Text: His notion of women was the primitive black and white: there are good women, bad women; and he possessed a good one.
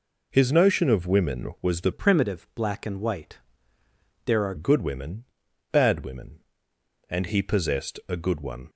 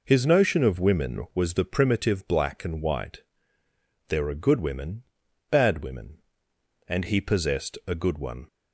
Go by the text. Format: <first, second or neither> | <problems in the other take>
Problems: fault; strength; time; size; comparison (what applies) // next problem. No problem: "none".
second | changes voice from "primitive" to "are"; from 1.9 to 4.5 s; 2.6 s long